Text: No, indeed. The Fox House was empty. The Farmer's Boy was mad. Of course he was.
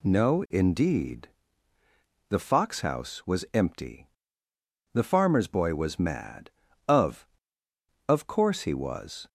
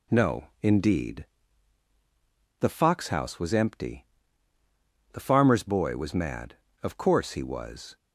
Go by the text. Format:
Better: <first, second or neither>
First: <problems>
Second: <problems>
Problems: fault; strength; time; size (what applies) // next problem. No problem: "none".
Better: second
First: says "Of" twice; at 8.0 s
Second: none